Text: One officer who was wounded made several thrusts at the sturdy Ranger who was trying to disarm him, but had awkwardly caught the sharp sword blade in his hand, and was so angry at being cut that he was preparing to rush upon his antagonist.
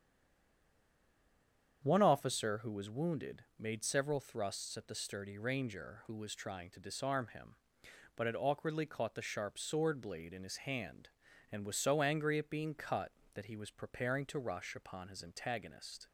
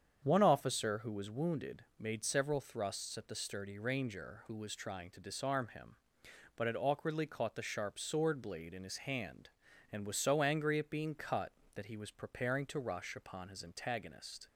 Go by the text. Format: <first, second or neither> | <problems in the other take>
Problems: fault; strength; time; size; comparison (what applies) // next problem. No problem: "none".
second | stays silent before the first word; noticeable; until 1.8 s; 1.8 s long // starts louder than the rest; strong; until 2.8 s; 8 dB; strong in the second // pauses between "wounded" and "made"; slight; at 3.4 s; 0.16 s long; slight in the second